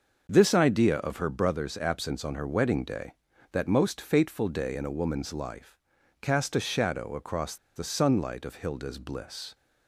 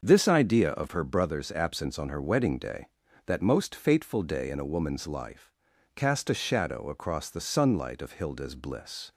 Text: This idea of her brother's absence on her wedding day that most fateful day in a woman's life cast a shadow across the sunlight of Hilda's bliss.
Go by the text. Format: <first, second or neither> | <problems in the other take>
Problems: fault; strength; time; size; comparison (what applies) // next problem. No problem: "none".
second | starts louder than the rest; until 1.2 s; 6 dB; also in the second // pauses between "life" and "cast"; at 5.7 s; 0.44 s long; also in the second // pauses between "across" and "the"; slight; at 7.5 s; 0.20 s long